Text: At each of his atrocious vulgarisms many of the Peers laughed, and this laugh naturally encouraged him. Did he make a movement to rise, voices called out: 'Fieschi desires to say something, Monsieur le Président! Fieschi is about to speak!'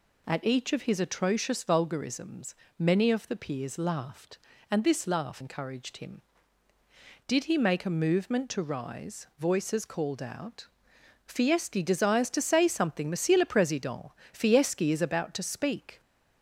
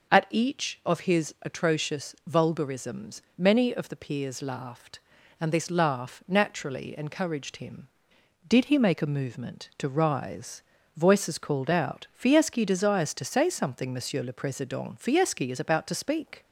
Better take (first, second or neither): second